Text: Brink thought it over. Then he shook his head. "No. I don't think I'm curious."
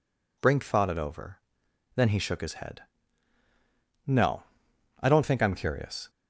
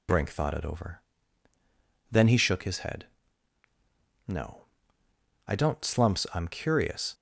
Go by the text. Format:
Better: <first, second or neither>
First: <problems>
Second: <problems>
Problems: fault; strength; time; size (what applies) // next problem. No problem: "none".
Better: first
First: none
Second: says "slumps" for "think"; at 5.8 s